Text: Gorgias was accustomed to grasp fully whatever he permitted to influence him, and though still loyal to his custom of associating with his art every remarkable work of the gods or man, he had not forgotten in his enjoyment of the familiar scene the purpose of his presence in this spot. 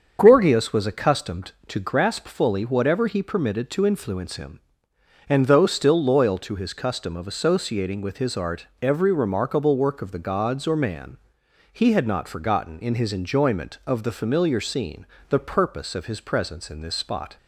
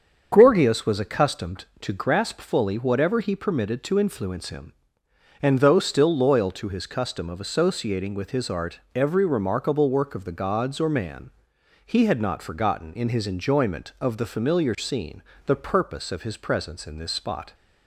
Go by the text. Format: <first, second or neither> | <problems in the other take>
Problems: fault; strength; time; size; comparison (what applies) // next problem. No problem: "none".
neither | starts louder than the rest; the same in both // pauses between "art" and "every"; slight; the same in both // pauses between "scene" and "the"; slight; the same in both